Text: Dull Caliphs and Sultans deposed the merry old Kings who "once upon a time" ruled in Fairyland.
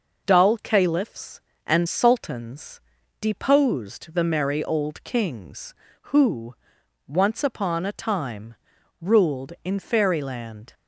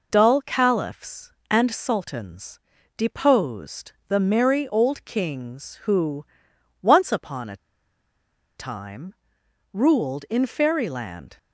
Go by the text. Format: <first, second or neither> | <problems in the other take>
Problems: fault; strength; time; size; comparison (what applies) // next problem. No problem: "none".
first | pauses between "Sultans" and "deposed"; at 2.5 s; 0.40 s long; also in the first // pauses between "deposed" and "the"; slight; at 3.9 s; 0.16 s long // pauses between "who" and "once"; noticeable; at 6.2 s; 0.56 s long; noticeable in the first // pauses between "a" and "time"; at 7.5 s; 1.0 s long // pauses between "time" and "ruled"; noticeable; at 9.1 s; 0.58 s long; also in the first